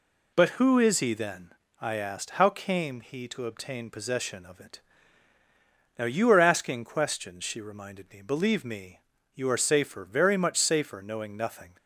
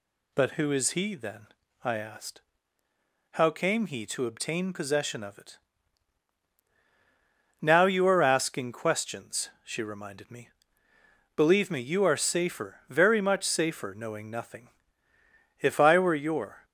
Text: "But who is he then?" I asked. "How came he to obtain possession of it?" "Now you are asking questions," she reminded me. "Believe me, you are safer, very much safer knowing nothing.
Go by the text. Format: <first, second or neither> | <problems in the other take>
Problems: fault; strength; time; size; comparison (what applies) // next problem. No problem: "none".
first | goes on to say "If I were your"; noticeable; from 15.5 s on; 1.0 s long